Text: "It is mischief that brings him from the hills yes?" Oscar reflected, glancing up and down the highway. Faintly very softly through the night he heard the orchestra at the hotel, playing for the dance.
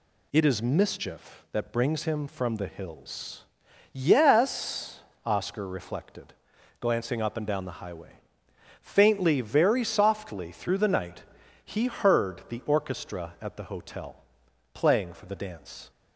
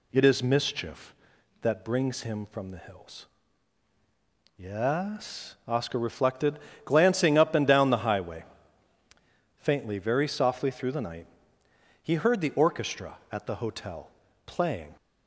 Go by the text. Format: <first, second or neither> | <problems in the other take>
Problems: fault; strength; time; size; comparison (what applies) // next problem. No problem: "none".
first | pauses between "hills" and "yes"; strong; at 3.2 s; 1.3 s long; noticeable in the first // pauses between "night" and "he"; noticeable; at 11.2 s; 0.76 s long; also in the first // stops before "for the dance"; at 14.9 s